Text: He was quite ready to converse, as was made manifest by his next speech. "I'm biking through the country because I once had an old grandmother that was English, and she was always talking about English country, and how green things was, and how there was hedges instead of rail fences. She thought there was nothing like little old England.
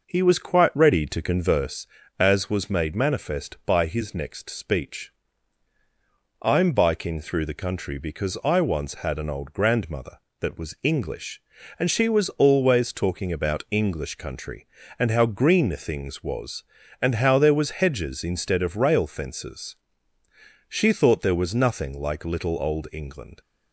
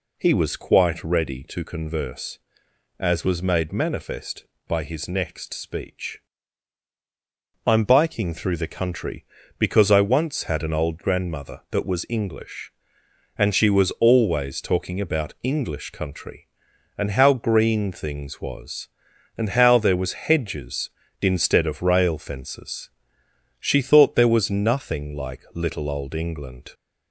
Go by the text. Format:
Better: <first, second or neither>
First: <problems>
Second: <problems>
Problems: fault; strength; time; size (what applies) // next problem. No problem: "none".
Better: second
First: starts louder than the rest; noticeable; until 1.8 s; 5.5 dB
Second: none